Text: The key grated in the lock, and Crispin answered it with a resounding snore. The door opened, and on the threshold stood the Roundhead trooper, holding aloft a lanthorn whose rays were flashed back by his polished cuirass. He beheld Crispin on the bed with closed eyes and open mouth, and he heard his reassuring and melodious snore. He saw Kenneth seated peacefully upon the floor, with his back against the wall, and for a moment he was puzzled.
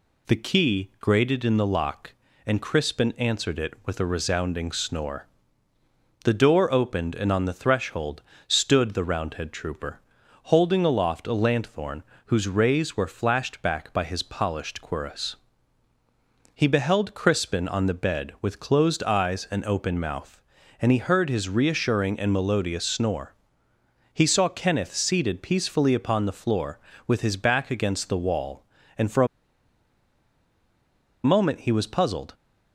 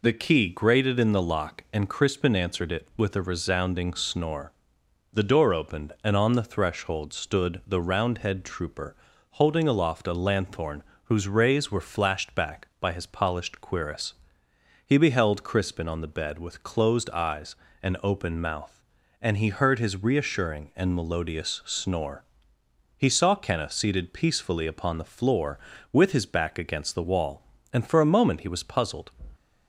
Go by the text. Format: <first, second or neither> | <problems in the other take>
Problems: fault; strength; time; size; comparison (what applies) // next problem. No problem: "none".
second | pauses between "threshold" and "stood"; slight; at 8.2 s; 0.24 s long // pauses between "lanthorn" and "whose"; slight; at 12.0 s; 0.26 s long; slight in the second // pauses between "a" and "moment"; strong; at 29.2 s; 1.9 s long